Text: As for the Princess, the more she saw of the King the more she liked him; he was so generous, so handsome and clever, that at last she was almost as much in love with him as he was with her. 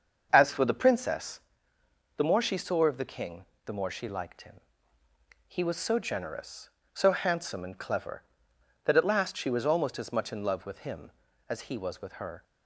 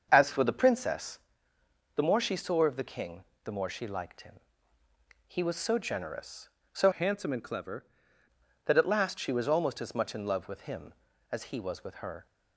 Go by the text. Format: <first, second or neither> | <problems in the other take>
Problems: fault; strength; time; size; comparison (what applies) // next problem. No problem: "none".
first | starts louder than the rest; until 1.1 s; 7 dB; also in the first // pauses between "King" and "the"; slight; at 3.2 s; 0.20 s long; slight in the first // changes voice from "handsome" to "clever"; from 6.9 to 7.8 s; 0.9 s long